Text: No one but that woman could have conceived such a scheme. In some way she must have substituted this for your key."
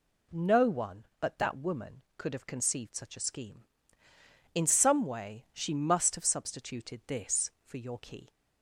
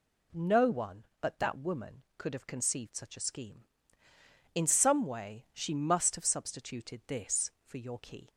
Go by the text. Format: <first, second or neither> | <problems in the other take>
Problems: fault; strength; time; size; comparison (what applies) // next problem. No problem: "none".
neither | none